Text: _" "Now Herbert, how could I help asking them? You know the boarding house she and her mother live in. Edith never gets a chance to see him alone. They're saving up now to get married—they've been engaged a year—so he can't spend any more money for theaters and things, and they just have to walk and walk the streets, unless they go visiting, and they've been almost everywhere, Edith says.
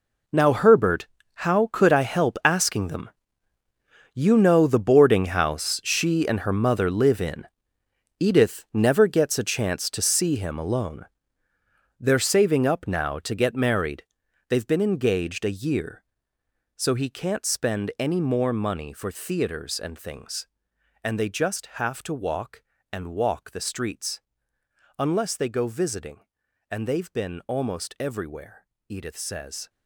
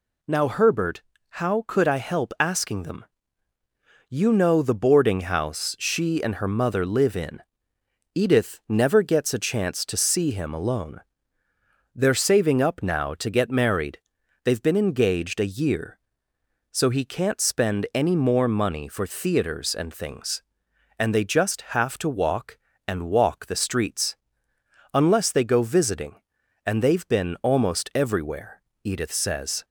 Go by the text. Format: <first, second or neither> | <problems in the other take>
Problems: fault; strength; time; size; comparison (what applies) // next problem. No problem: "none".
second | gets quieter; strong; throughout; 14.5 dB